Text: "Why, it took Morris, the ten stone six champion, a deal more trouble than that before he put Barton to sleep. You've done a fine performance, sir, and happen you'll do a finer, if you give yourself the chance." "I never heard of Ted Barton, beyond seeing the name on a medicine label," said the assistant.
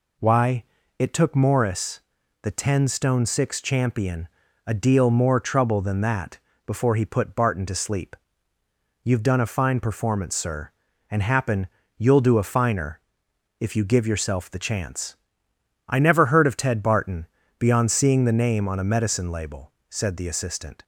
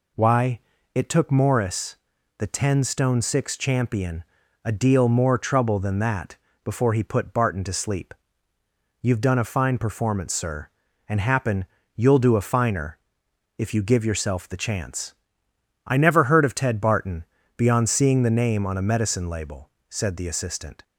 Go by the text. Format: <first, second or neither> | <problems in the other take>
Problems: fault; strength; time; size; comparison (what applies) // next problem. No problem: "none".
neither | pauses between "that" and "before"; slight; the same in both // pauses between "happen" and "you'll"; slight; the same in both